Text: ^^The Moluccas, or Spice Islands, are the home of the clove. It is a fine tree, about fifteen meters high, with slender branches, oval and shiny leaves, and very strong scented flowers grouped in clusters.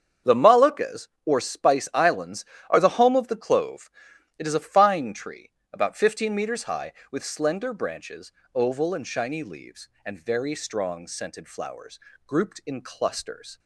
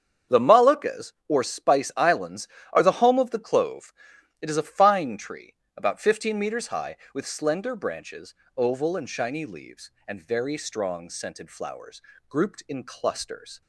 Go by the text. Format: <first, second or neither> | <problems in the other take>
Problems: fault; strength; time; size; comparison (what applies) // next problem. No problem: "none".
neither | starts louder than the rest; strong; the same in both // pauses between "flowers" and "grouped"; slight; the same in both